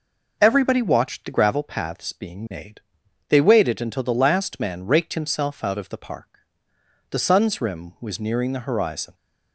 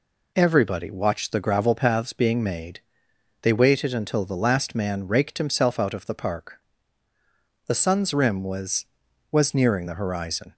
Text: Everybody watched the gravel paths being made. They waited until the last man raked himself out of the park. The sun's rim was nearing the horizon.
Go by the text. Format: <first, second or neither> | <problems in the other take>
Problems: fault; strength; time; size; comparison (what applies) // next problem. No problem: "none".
first | says "was" twice; at 9.3 s